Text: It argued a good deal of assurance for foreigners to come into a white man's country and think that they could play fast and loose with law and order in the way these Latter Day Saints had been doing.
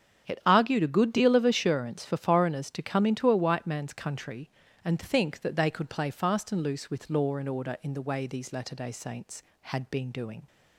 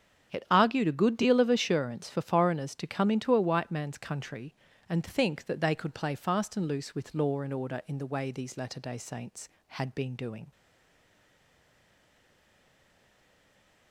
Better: first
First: starts louder than the rest; strong; until 1.2 s; 8 dB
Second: starts louder than the rest; strong; until 1.3 s; 8.5 dB // stays silent after the last word; strong; from 10.5 s on; 3.4 s long

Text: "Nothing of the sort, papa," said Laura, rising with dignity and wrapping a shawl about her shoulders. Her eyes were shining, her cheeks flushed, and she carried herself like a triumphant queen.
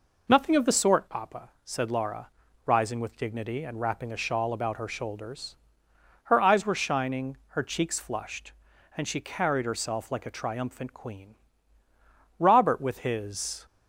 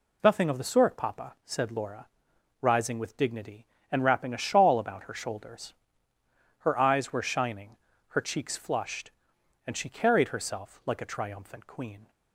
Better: second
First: goes on to say "Robert with his"; noticeable; from 12.3 s on; 1.2 s long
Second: none

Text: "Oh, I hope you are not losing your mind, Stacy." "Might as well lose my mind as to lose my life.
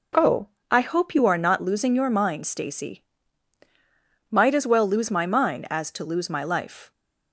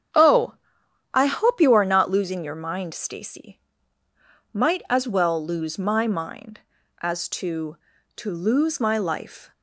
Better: first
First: none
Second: starts louder than the rest; strong; until 1.7 s; 8.5 dB // says "to" twice; at 8.1 s

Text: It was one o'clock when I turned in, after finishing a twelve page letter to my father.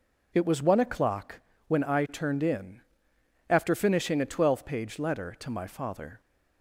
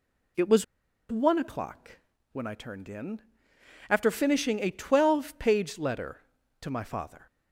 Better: first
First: pauses between "o'clock" and "when"; slight; at 1.4 s; 0.28 s long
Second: pauses between "was" and "one"; noticeable; at 0.6 s; 0.47 s long // pauses between "o'clock" and "when"; slight; at 1.9 s; 0.34 s long

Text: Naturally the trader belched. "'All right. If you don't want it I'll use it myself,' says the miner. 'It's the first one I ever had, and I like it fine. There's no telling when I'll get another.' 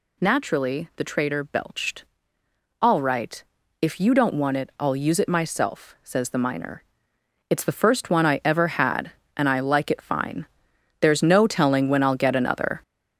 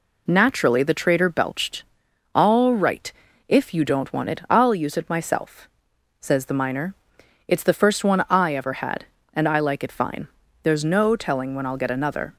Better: second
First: gets louder; throughout; 6.5 dB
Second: none

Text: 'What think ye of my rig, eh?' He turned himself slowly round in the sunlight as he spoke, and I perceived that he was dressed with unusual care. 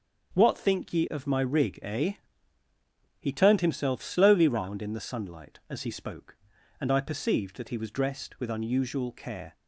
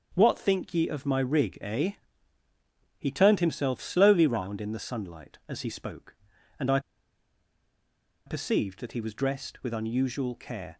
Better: first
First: starts louder than the rest; until 1.3 s; 7 dB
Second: starts louder than the rest; until 1.1 s; 7 dB // pauses between "I" and "perceived"; strong; at 6.7 s; 1.4 s long

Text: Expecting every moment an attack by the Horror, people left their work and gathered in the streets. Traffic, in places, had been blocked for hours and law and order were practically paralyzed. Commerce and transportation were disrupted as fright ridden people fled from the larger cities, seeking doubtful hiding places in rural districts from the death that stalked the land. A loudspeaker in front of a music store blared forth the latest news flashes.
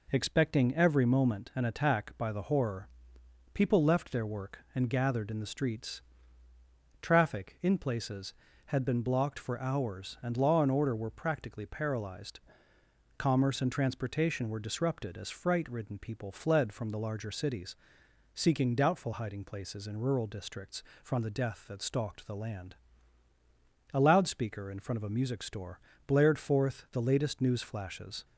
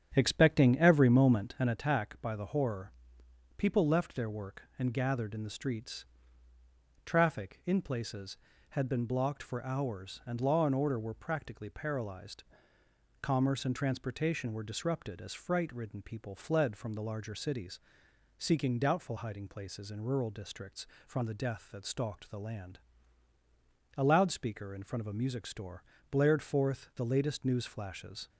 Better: first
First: pauses between "store" and "blared"; slight; at 25.7 s; 0.28 s long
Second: starts louder than the rest; strong; until 1.8 s; 9 dB // pauses between "store" and "blared"; slight; at 25.8 s; 0.28 s long

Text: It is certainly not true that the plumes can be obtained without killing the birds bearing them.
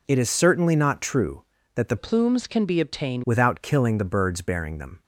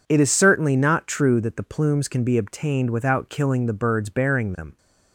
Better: second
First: changes voice from "plumes" to "obtained"; from 1.9 to 3.2 s; 1.3 s long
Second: none

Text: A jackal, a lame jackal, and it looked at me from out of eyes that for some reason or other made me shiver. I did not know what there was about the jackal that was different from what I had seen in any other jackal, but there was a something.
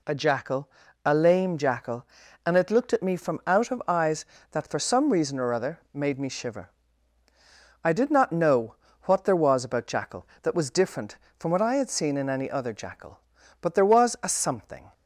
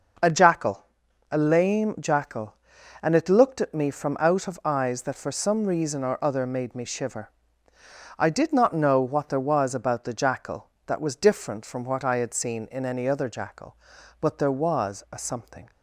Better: second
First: pauses between "know" and "what"; slight; at 8.7 s; 0.28 s long // skips "the"; at 9.8 s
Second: none

